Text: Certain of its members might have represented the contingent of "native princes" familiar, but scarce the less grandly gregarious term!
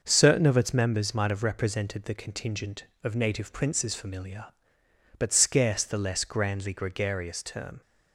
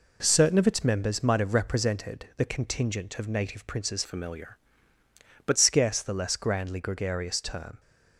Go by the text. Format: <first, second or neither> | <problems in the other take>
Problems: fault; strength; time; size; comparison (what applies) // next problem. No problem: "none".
first | changes voice from "familiar" to "but"; from 4.0 to 5.5 s; 1.5 s long